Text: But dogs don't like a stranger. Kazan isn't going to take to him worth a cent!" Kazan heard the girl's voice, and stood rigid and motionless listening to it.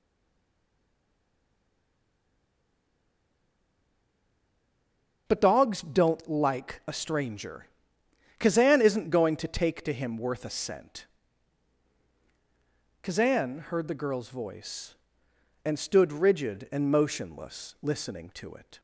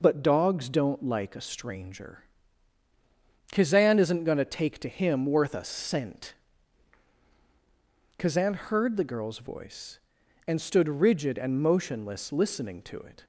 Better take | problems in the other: second | stays silent before the first word; strong; until 5.2 s; 5.2 s long // starts louder than the rest; noticeable; until 6.2 s; 6 dB

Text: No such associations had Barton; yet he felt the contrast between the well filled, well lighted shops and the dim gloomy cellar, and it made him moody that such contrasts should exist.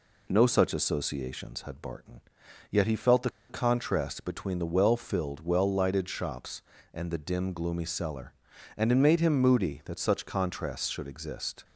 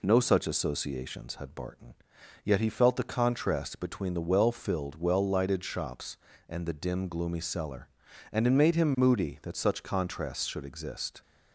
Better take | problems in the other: second | pauses between "the" and "contrast"; slight; at 3.2 s; 0.19 s long

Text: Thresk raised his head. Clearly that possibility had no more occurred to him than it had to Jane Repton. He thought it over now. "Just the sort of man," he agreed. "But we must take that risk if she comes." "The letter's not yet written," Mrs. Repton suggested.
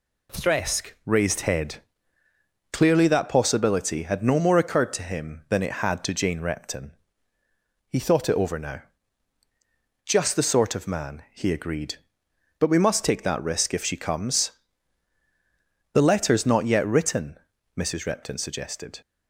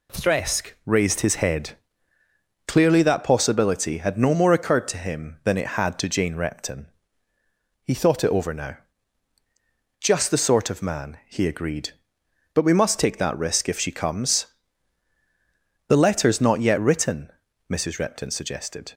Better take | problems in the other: second | skips "his"; at 1.4 s

